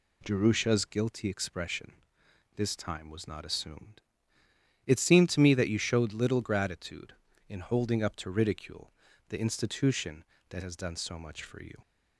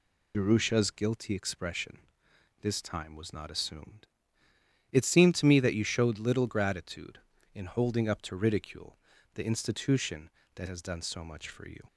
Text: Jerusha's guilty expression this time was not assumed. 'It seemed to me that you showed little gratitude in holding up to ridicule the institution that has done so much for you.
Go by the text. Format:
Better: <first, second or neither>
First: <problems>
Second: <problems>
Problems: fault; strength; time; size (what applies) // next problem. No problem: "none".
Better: first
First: pauses between "expression" and "this"; noticeable; at 1.9 s; 0.62 s long // pauses between "ridicule" and "the"; slight; at 8.9 s; 0.36 s long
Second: loses the start of "Jerusha's"; at 0.3 s; 85 ms // pauses between "expression" and "this"; noticeable; at 1.9 s; 0.62 s long // pauses between "ridicule" and "the"; slight; at 8.9 s; 0.36 s long